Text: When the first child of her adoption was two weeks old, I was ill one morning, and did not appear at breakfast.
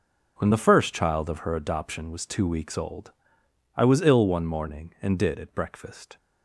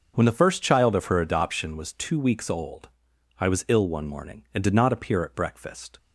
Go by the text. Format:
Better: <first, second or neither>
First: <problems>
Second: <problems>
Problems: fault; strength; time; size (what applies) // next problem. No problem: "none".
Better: second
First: skips "not appear"; at 5.3 s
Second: none